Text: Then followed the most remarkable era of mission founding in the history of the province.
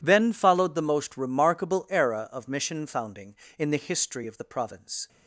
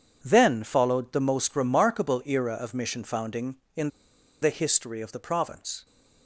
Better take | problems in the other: first | pauses between "in" and "the"; noticeable; at 3.8 s; 0.52 s long

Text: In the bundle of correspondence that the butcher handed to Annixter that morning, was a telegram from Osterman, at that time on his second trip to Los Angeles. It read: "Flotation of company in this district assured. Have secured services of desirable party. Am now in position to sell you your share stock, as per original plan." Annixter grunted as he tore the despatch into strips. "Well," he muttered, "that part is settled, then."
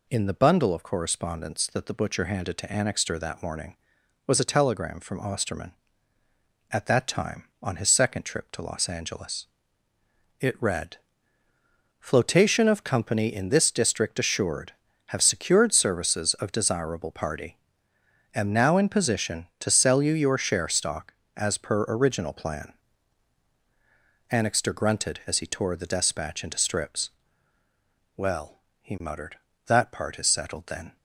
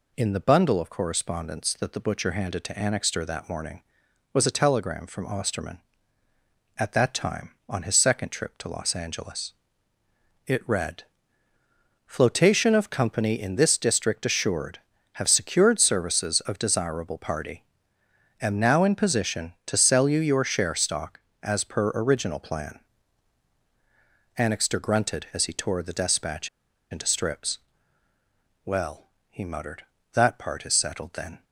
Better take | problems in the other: first | pauses between "despatch" and "into"; at 26.4 s; 0.43 s long

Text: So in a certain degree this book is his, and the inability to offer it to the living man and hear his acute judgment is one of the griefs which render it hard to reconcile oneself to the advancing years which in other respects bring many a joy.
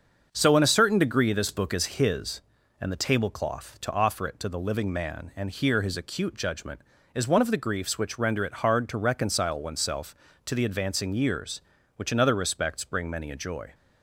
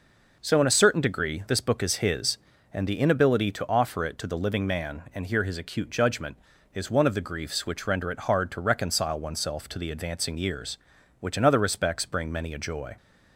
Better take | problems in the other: second | starts louder than the rest; until 1.3 s; 6.5 dB // says "tablecloth" for "inability"; at 3.0 s

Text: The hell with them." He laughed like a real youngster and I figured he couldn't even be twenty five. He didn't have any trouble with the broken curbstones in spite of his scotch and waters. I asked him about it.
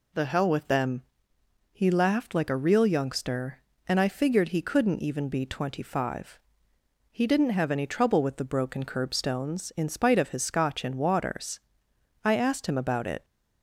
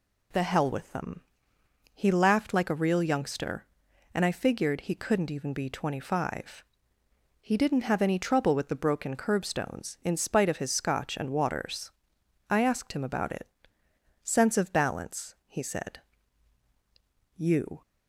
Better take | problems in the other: first | goes on to say "Sense of balance he said You"; strong; from 14.2 s on; 3.6 s long

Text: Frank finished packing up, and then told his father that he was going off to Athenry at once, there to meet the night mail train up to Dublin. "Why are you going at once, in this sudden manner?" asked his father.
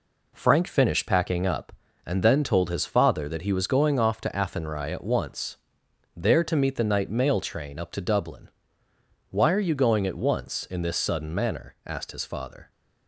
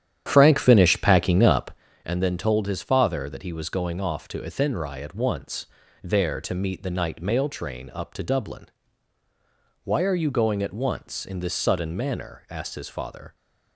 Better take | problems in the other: first | starts louder than the rest; strong; until 2.0 s; 10 dB

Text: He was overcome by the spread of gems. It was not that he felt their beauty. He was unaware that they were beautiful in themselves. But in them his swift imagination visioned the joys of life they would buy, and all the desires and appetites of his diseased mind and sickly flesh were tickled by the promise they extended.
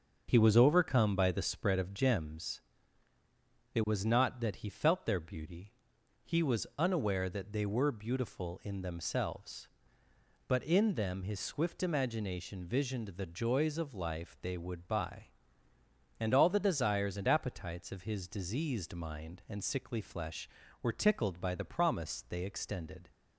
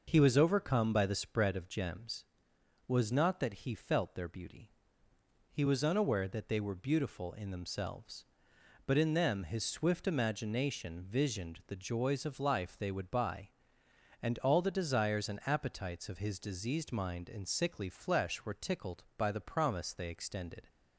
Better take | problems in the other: first | starts louder than the rest; noticeable; until 1.0 s; 6 dB; also in the first // skips "It"; at 2.5 s

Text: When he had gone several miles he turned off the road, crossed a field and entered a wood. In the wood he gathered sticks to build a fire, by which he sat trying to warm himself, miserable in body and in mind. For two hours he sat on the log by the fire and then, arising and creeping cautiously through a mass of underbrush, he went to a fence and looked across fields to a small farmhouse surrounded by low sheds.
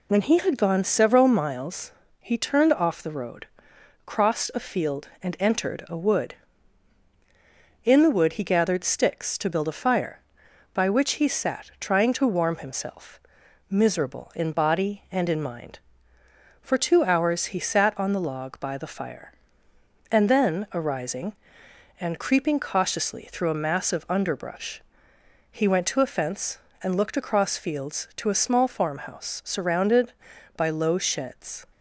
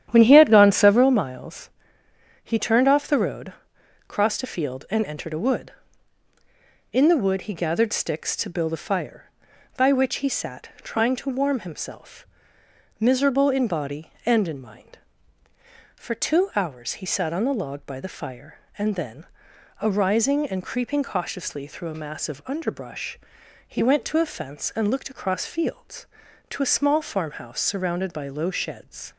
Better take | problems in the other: first | starts louder than the rest; strong; until 1.1 s; 10.5 dB // pauses between "miles" and "he"; noticeable; at 1.6 s; 0.72 s long; slight in the first

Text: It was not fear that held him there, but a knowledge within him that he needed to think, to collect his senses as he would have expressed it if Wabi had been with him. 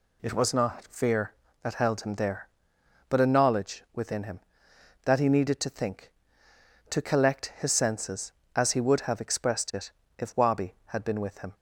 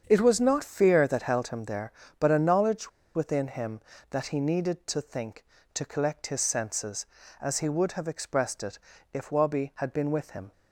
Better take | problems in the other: first | starts louder than the rest; strong; until 1.0 s; 7.5 dB // pauses between "knowledge" and "within"; slight; at 2.8 s; 0.25 s long // pauses between "it" and "if"; slight; at 8.7 s; 0.34 s long; slight in the first

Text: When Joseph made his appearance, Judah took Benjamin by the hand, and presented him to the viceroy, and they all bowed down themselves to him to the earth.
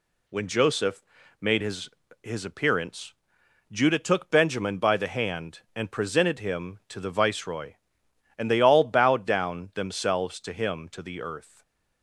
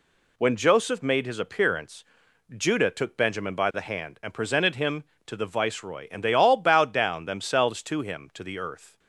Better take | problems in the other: second | pauses between "Joseph" and "made"; slight; at 1.0 s; 0.36 s long // says "his" twice; at 2.2 s // stays silent after the last word; slight; from 11.4 s on; 0.6 s long

